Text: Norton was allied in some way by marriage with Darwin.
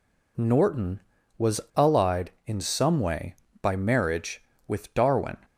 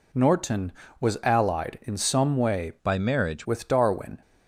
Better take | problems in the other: first | changes voice from "by" to "marriage"; from 2.8 to 3.4 s; 0.6 s long

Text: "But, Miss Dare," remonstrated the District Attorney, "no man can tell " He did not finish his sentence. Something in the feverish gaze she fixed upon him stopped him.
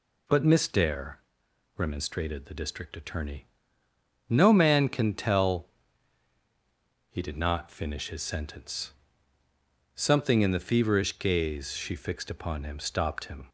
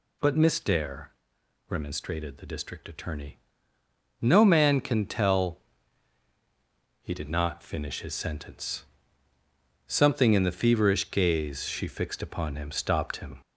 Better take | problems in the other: first | gets louder; slight; throughout; 3 dB

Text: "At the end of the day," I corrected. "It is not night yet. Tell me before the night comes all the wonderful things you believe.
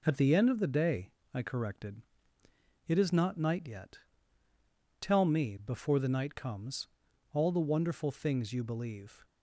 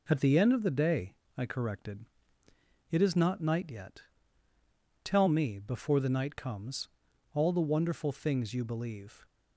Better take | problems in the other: neither | pauses between "comes" and "all"; noticeable; the same in both

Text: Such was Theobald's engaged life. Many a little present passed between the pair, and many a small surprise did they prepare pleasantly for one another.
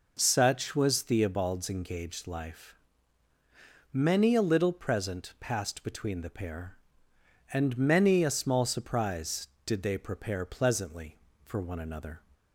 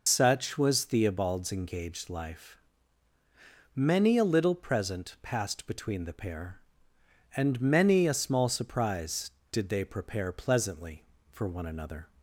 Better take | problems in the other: first | loses the start of "Such"; at 0.0 s; 75 ms

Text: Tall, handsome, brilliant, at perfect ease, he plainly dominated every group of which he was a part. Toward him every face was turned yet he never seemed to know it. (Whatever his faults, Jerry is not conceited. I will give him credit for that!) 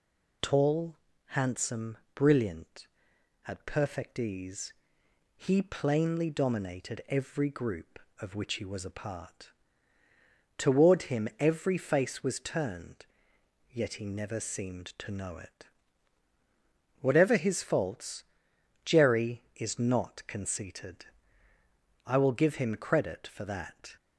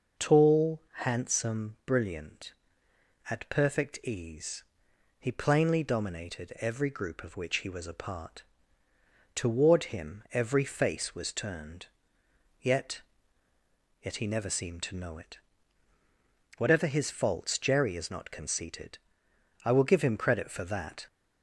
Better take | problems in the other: first | pauses between "turned" and "yet"; noticeable; at 11.8 s; 0.74 s long; noticeable in the first // says "yet" twice; at 14.0 s

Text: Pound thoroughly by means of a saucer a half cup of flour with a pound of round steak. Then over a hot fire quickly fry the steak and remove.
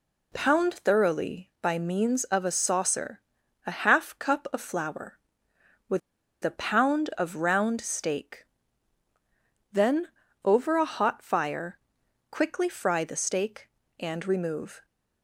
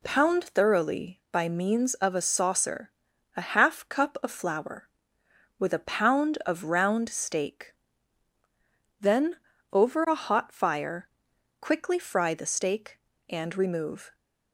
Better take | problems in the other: second | pauses between "saucer" and "a"; noticeable; at 3.2 s; 0.46 s long; noticeable in the second // pauses between "with" and "a"; at 5.9 s; 0.44 s long // pauses between "Then" and "over"; slight; at 10.0 s; 0.34 s long; slight in the second // pauses between "fire" and "quickly"; noticeable; at 11.7 s; 0.50 s long; noticeable in the second

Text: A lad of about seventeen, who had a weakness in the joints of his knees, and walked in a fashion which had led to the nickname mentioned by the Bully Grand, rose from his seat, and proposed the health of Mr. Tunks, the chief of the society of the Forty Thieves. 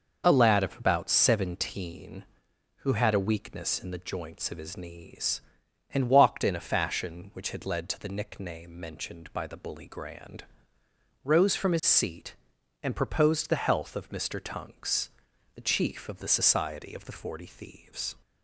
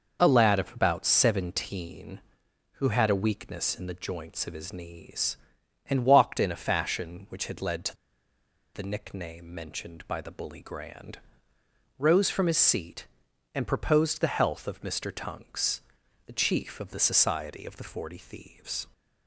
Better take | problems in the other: first | pauses between "to" and "the"; noticeable; at 7.9 s; 0.80 s long

